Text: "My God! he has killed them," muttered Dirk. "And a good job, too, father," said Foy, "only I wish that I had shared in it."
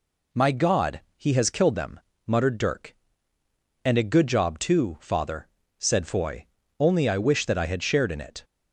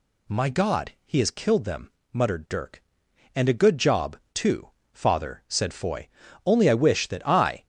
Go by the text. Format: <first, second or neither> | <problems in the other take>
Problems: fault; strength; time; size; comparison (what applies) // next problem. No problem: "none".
first | stops before "had shared in it"; at 7.6 s